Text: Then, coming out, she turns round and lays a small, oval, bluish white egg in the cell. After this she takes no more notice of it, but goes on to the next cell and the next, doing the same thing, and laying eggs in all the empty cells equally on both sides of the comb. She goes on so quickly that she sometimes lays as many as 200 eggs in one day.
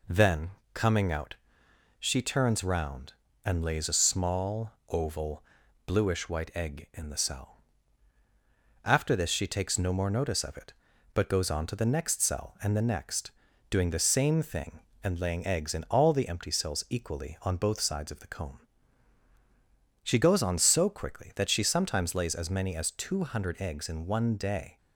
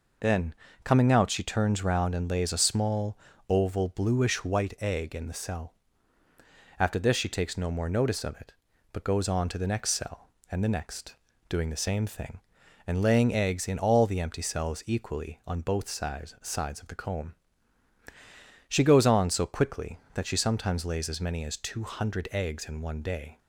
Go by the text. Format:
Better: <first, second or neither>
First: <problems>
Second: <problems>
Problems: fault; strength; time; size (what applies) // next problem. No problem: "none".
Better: first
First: none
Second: says "sides" twice; at 16.4 s